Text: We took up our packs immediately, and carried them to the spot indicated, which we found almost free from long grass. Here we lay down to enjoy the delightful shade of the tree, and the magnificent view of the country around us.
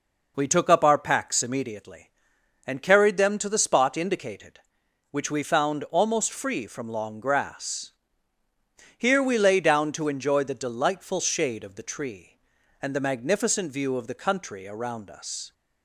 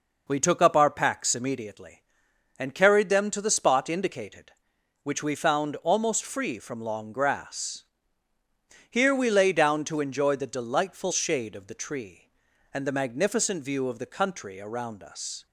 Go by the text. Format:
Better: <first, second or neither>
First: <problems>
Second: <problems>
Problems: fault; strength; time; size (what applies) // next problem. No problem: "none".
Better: neither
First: none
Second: none